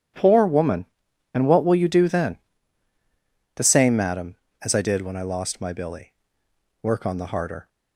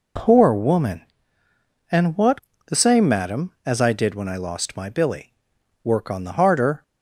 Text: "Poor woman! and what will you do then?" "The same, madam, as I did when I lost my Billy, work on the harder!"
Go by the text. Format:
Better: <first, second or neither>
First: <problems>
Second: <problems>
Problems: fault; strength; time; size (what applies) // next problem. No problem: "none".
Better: first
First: none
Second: skips "will you do then"; at 2.5 s